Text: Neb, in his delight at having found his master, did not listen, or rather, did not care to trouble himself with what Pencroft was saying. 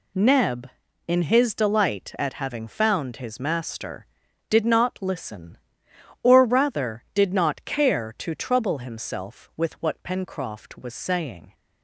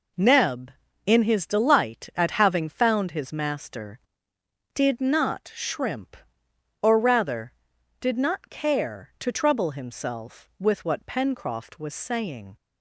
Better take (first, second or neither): first